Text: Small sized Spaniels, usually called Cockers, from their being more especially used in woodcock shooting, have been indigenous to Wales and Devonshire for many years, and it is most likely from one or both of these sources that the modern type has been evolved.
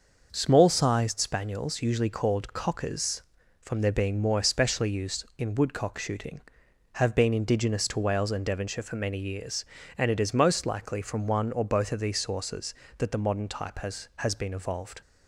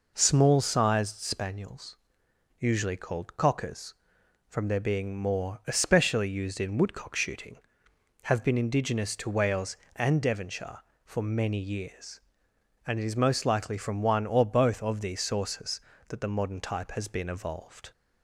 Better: second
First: starts louder than the rest; noticeable; until 1.3 s; 6 dB // says "has" twice; at 14.1 s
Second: none

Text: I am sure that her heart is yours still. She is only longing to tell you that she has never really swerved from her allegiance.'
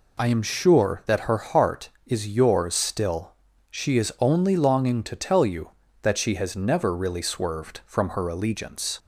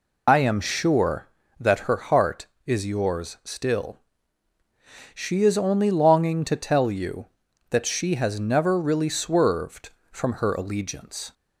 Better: first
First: none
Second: loses the start of "I"; at 0.2 s; 115 ms

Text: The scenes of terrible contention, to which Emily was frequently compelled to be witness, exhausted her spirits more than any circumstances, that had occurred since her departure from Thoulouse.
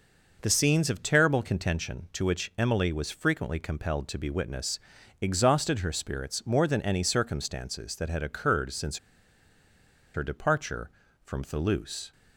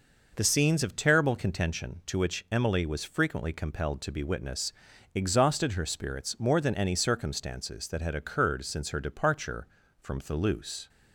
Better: second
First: pauses between "since" and "her"; at 8.9 s; 1.1 s long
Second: none

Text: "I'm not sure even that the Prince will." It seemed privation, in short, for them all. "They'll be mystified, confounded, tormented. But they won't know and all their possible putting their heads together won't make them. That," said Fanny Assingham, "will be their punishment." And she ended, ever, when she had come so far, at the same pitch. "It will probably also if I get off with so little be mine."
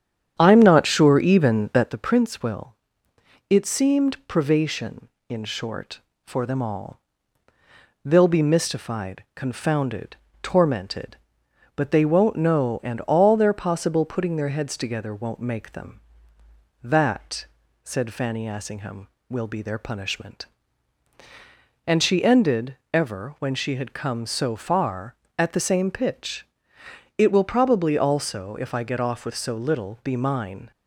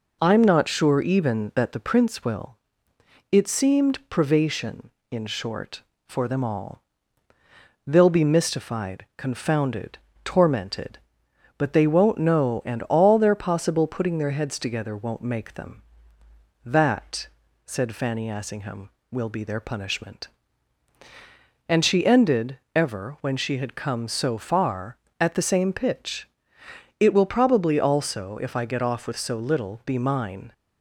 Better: second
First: starts louder than the rest; strong; until 1.9 s; 9 dB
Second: none

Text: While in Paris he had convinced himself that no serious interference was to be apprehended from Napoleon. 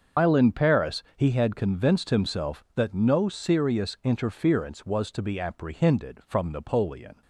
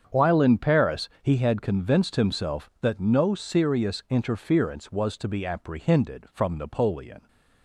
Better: second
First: loses the start of "While"; at 0.1 s; 165 ms // starts louder than the rest; until 1.3 s; 6.5 dB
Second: starts louder than the rest; strong; until 1.2 s; 7.5 dB

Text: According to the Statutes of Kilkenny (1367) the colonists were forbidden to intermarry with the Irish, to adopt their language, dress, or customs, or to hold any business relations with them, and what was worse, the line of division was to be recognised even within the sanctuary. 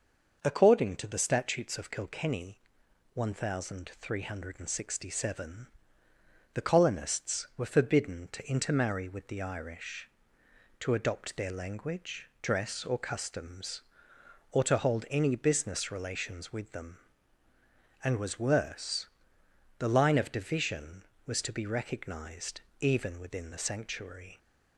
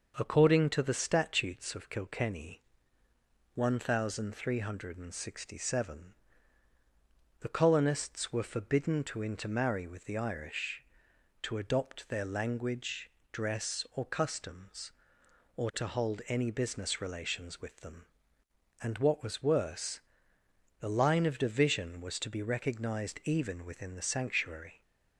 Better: second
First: starts louder than the rest; noticeable; until 1.4 s; 6 dB // skips "what"; at 18.1 s // pauses between "recognised" and "even"; slight; at 22.6 s; 0.18 s long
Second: starts louder than the rest; until 1.1 s; 6 dB

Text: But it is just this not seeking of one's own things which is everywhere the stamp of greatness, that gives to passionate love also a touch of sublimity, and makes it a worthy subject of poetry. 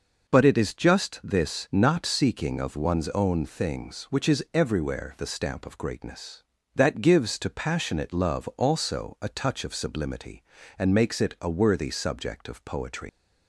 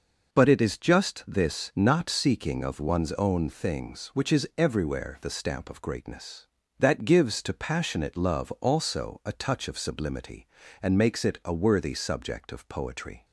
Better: second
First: leaves "poetry" unfinished; at 13.0 s; 115 ms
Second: none

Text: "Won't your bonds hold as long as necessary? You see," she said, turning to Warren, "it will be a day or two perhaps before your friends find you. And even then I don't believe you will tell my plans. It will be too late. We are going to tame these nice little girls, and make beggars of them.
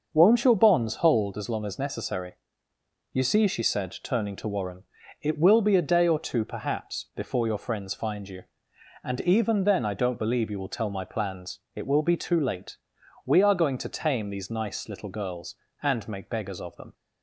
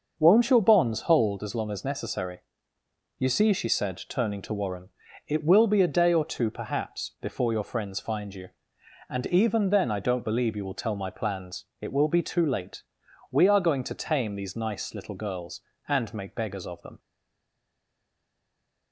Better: first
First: starts louder than the rest; noticeable; until 1.1 s; 6 dB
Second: starts louder than the rest; noticeable; until 1.1 s; 6 dB // stays silent after the last word; noticeable; from 16.9 s on; 2.0 s long

